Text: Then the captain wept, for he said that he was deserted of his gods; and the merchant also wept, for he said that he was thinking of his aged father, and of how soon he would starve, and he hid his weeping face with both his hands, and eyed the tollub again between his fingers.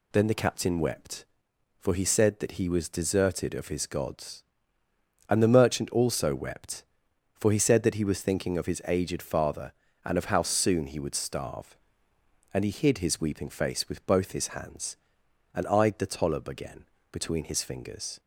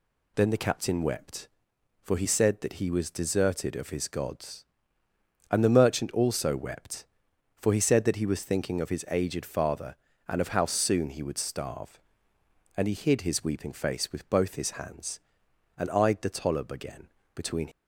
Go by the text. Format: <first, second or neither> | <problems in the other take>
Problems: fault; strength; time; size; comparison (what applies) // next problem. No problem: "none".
first | pauses between "again" and "between"; slight; at 17.0 s; 0.26 s long; slight in the first // stops before "his fingers"; at 17.7 s